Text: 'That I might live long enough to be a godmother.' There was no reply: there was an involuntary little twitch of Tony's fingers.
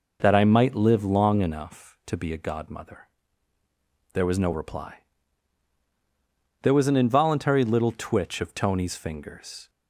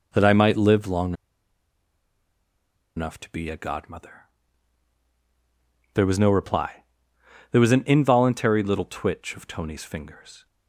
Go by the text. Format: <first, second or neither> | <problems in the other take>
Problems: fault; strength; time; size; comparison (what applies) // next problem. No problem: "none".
first | pauses between "long" and "enough"; strong; at 1.1 s; 1.8 s long